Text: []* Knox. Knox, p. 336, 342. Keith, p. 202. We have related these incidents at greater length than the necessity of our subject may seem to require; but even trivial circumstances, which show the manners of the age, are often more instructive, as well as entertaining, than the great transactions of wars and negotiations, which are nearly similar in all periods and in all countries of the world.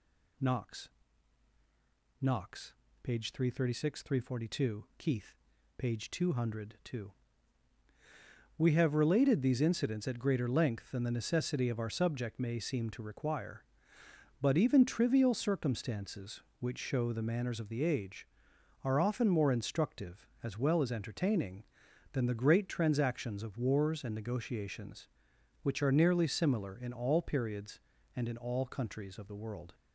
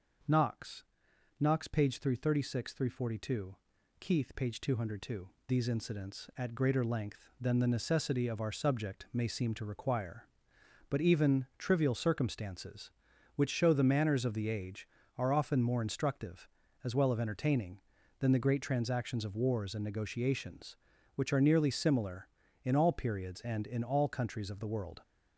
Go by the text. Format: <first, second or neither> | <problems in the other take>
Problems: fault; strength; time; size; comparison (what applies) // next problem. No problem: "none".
first | starts louder than the rest; until 1.8 s; 6.5 dB // skips "We have related"; at 5.3 s